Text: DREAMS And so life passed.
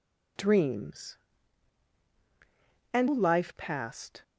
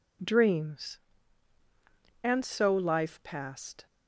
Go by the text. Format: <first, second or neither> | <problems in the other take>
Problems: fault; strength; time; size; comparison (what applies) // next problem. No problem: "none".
second | skips "so"; at 3.0 s